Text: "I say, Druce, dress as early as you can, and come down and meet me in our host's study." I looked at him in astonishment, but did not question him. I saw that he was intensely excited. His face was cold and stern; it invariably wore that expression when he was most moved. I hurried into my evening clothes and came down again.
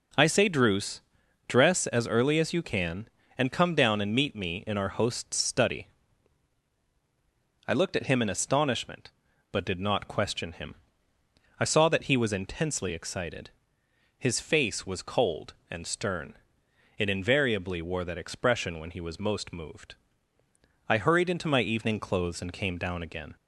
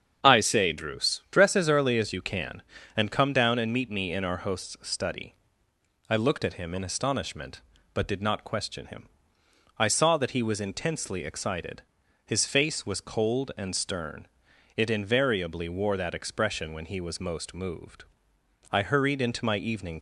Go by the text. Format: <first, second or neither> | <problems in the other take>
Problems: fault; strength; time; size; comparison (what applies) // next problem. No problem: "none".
first | starts louder than the rest; strong; until 1.3 s; 7.5 dB // stops before "clothes and came down again"; at 19.9 s